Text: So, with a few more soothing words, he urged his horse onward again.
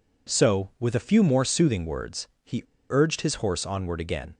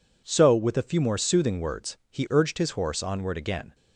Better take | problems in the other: second | pauses between "he" and "urged"; slight; at 2.6 s; 0.28 s long

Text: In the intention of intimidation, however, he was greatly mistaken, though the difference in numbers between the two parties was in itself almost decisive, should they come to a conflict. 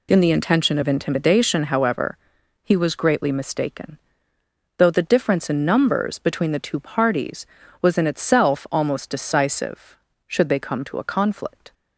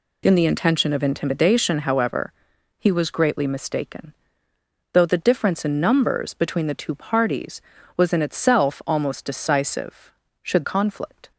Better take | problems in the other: first | skips "they come to a"; at 10.6 s

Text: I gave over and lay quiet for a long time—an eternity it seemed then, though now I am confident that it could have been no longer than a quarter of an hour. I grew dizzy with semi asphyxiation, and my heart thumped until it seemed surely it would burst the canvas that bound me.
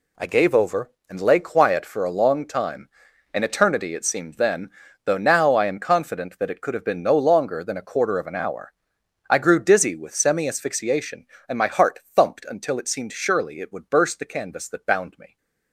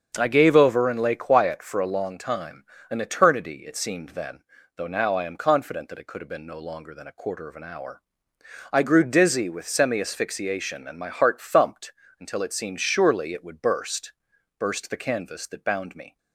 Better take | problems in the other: first | starts louder than the rest; until 1.1 s; 7 dB // pauses between "thumped" and "until"; slight; at 11.9 s; 0.26 s long // says "burst" twice; at 14.5 s

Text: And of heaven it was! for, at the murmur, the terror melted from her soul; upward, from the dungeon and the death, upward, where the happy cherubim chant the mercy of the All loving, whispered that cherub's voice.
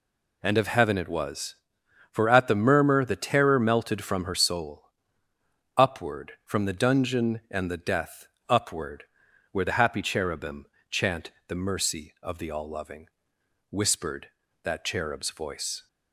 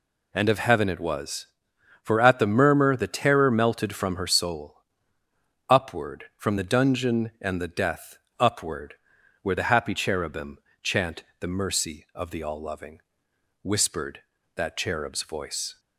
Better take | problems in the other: neither | pauses between "cherubim" and "chant"; slight; the same in both // pauses between "chant" and "the"; slight; the same in both

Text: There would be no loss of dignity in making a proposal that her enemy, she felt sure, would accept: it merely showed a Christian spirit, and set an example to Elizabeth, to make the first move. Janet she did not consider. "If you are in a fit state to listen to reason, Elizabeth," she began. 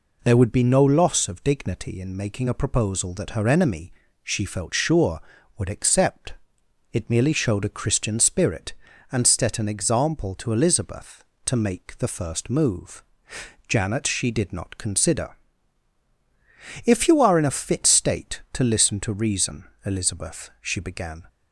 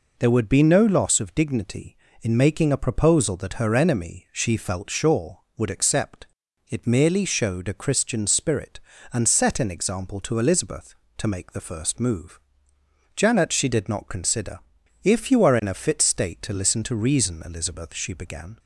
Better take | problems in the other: neither | none

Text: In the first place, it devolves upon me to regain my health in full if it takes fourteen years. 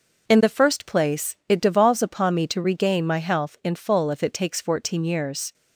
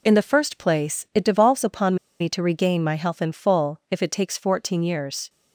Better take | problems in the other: first | pauses between "upon" and "me"; slight; at 1.9 s; 0.25 s long

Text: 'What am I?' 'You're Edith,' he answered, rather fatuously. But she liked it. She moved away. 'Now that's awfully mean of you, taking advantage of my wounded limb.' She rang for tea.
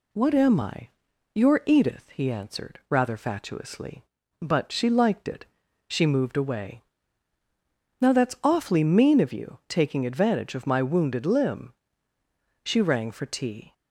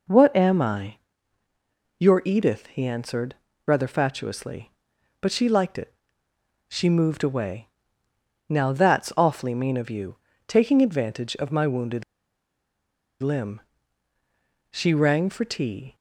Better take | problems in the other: first | pauses between "wounded" and "limb"; at 12.0 s; 1.1 s long

